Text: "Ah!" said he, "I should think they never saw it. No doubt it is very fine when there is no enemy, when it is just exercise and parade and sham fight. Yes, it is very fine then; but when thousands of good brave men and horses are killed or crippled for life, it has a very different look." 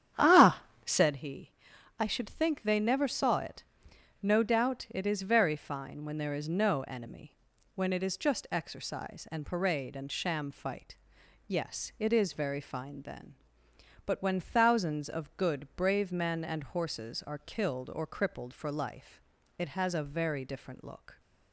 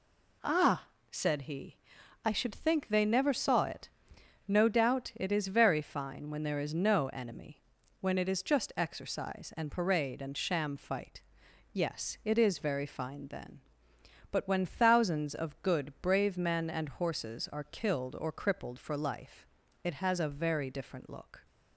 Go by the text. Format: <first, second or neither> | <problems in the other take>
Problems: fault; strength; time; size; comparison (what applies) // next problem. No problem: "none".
second | starts louder than the rest; strong; until 1.2 s; 9.5 dB